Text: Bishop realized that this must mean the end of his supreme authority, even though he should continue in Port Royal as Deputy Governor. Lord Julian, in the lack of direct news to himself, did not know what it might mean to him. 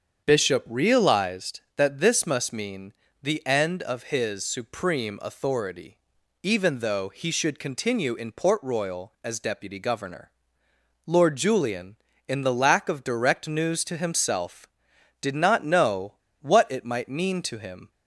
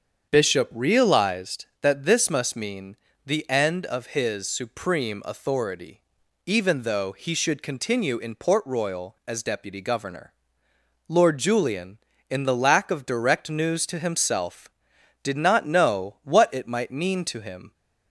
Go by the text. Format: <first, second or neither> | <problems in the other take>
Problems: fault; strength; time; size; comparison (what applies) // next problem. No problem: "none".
second | starts louder than the rest; strong; until 1.2 s; 7.5 dB; strong in the second // pauses between "mean" and "the"; slight; at 2.9 s; 0.30 s long; slight in the second // pauses between "know" and "what"; slight; at 16.1 s; 0.27 s long